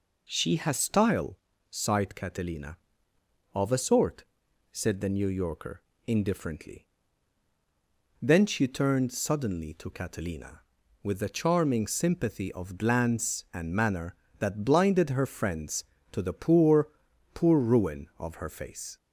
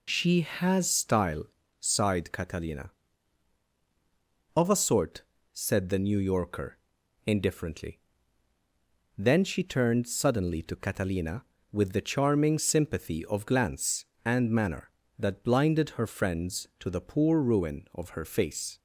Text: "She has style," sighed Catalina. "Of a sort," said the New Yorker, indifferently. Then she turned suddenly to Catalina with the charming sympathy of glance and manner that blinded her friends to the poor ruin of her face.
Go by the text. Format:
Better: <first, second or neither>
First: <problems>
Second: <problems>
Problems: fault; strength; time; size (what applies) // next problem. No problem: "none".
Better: second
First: says "poor" twice; at 17.3 s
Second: none